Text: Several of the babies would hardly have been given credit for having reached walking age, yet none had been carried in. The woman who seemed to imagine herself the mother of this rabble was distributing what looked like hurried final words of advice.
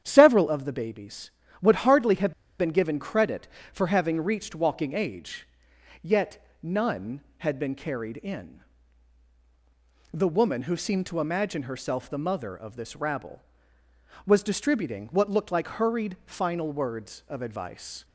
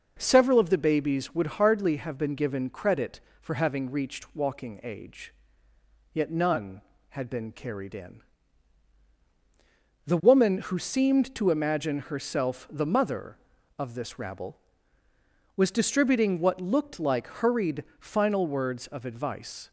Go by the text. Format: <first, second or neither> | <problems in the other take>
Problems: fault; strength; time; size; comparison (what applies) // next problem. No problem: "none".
second | starts louder than the rest; strong; until 1.0 s; 9.5 dB // pauses between "have" and "been"; slight; at 2.3 s; 0.26 s long // pauses between "yet" and "none"; slight; at 6.4 s; 0.16 s long